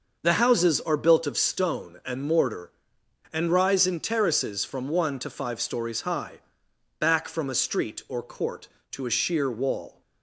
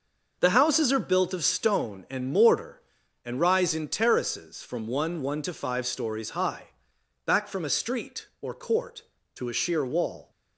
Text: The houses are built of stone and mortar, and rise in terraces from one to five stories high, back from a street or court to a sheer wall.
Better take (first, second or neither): first